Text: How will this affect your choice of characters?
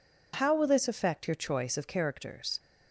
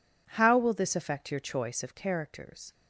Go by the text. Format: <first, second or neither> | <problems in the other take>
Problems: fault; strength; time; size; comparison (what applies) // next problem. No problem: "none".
neither | none